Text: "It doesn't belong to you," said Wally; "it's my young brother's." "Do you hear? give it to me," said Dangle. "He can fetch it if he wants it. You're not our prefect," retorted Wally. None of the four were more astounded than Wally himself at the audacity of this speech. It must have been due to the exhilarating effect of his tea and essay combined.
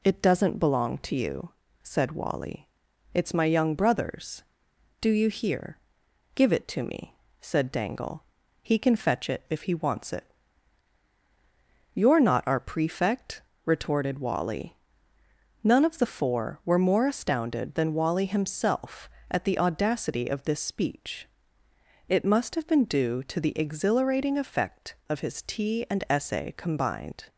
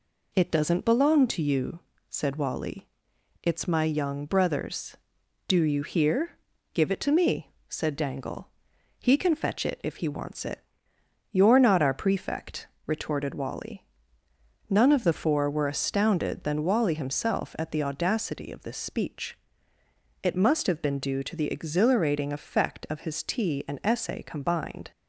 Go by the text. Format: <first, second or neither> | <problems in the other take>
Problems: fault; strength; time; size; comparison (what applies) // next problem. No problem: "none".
first | skips "more"; at 15.6 s